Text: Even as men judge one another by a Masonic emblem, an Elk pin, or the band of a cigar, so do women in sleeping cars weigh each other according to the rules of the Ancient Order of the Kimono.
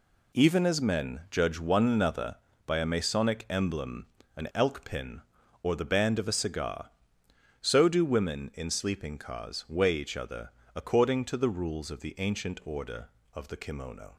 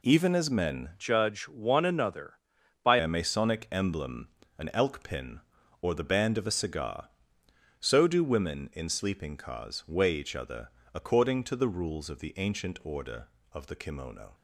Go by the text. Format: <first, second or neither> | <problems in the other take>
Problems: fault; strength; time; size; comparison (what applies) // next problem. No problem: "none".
first | changes voice from "judge" to "by"; from 0.9 to 2.9 s; 2.0 s long // pauses between "other" and "according"; slight; at 10.6 s; 0.26 s long; slight in the first